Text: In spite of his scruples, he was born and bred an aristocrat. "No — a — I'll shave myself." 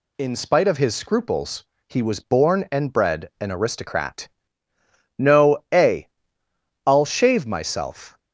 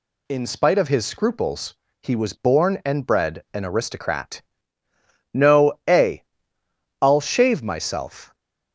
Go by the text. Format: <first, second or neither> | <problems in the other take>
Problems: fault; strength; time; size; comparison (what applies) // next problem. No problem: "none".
neither | none